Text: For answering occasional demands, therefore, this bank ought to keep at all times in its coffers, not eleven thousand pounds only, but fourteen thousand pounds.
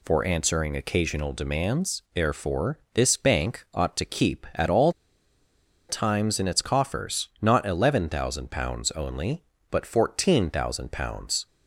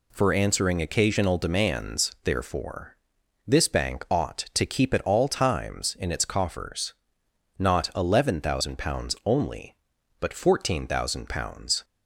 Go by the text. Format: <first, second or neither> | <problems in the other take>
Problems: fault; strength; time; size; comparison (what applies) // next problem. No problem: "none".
second | pauses between "all" and "times"; noticeable; at 4.9 s; 0.97 s long